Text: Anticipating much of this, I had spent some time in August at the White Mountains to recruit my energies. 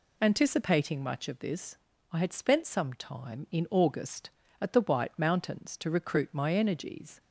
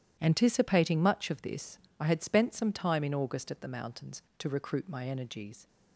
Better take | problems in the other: first | starts louder than the rest; strong; until 1.2 s; 11.5 dB // skips "White"; at 3.6 s

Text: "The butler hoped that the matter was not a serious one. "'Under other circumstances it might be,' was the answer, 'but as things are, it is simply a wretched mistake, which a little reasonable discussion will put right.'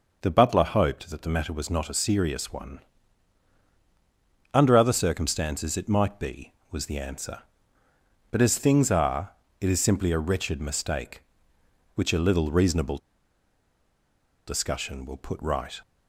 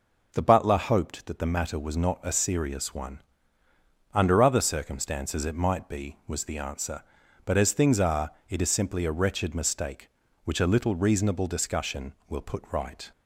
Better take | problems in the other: second | pauses between "reasonable" and "discussion"; strong; at 12.9 s; 1.4 s long

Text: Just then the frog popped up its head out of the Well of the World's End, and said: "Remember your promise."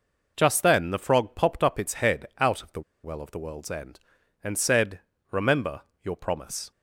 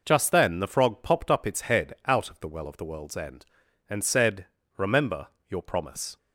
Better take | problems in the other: second | pauses between "the" and "Well"; slight; at 2.8 s; 0.23 s long // pauses between "Remember" and "your"; slight; at 5.8 s; 0.20 s long; slight in the second

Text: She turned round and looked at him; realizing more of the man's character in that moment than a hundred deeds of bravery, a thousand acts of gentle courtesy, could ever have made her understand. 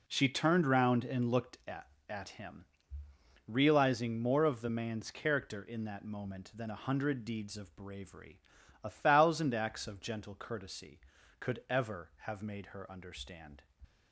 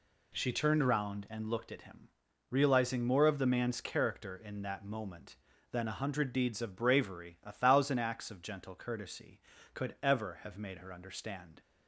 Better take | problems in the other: second | says "at" twice; at 2.0 s

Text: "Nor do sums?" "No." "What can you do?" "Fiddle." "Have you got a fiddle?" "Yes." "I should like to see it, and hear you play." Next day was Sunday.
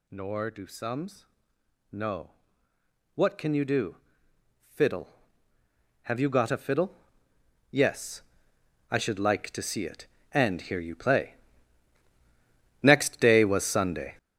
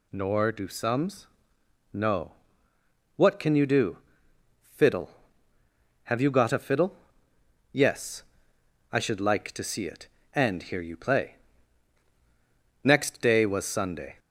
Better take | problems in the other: second | gets louder; strong; throughout; 8.5 dB

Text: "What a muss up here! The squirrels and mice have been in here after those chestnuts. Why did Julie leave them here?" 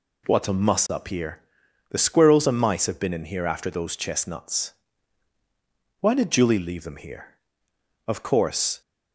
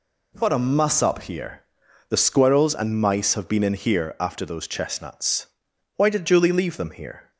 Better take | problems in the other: second | goes on to say "Of course"; noticeable; from 8.0 s on; 0.72 s long

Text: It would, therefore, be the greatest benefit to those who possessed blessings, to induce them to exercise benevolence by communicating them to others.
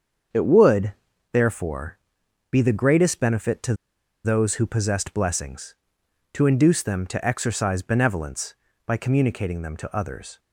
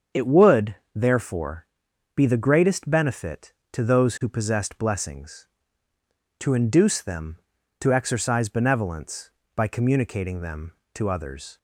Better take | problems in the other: second | starts louder than the rest; until 1.7 s; 7 dB; strong in the second // pauses between "to" and "those"; noticeable; at 3.7 s; 0.49 s long

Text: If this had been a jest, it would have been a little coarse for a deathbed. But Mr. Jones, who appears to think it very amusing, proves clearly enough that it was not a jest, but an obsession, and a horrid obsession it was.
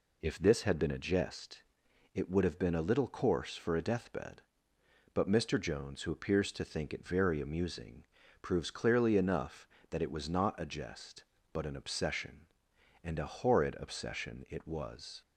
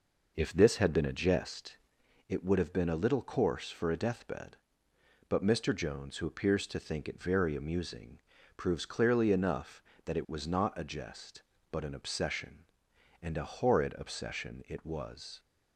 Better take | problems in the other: first | starts louder than the rest; noticeable; until 2.0 s; 5 dB

